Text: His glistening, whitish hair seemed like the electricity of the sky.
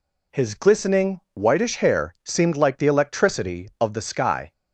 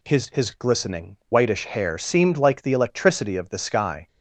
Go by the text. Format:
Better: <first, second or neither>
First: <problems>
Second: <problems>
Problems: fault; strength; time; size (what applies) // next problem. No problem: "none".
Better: first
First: none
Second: says "His" twice; at 0.3 s